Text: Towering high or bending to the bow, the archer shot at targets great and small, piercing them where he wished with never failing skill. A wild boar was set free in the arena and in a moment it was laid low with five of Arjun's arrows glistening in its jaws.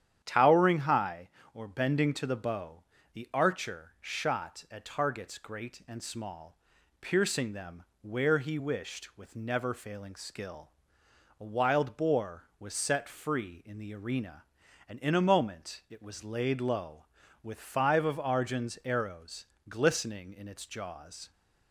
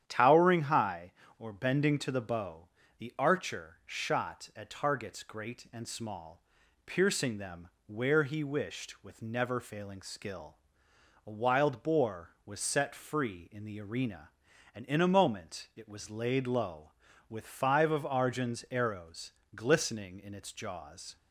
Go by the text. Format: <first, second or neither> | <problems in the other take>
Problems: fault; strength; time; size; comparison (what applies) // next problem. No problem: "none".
neither | starts louder than the rest; strong; the same in both // pauses between "them" and "where"; slight; the same in both // pauses between "arrows" and "glistening"; slight; the same in both